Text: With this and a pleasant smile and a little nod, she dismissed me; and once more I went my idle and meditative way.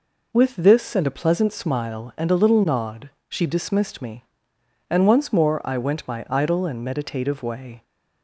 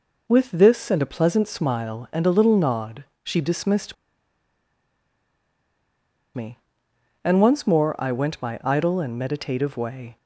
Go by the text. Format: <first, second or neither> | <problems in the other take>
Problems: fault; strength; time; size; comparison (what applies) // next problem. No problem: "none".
first | pauses between "dismissed" and "me"; strong; at 3.9 s; 2.3 s long